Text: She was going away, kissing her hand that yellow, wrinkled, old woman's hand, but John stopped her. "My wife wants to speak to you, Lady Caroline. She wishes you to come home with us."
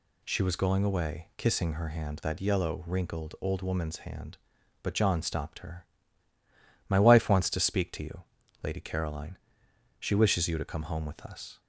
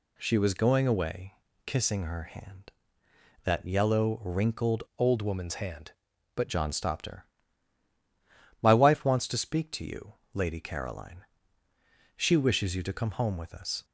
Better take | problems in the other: first | changes voice from "old" to "but"; from 4.9 to 6.4 s; 1.5 s long

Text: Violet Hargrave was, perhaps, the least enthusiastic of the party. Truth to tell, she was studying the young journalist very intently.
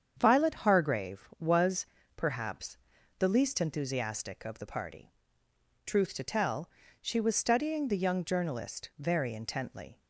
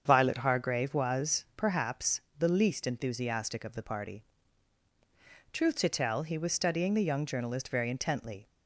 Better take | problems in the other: first | starts louder than the rest; strong; until 1.0 s; 7.5 dB; strong in the first // says "he" for "she"; at 6.2 s

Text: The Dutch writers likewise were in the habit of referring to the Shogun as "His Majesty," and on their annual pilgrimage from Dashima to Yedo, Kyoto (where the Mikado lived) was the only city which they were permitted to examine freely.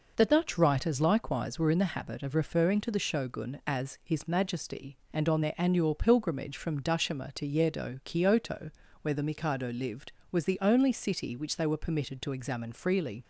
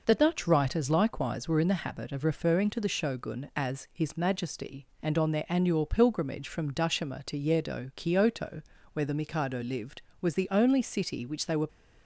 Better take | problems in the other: first | stops before "permitted to examine freely"; at 11.6 s

